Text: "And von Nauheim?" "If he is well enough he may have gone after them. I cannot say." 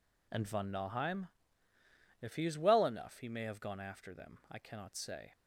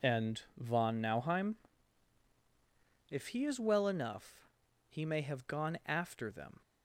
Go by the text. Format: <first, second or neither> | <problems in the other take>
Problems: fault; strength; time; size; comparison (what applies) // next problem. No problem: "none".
first | pauses between "And" and "von"; slight; at 0.4 s; 0.16 s long // pauses between "enough" and "he"; at 4.4 s; 0.40 s long // stops before "I cannot say"; at 6.6 s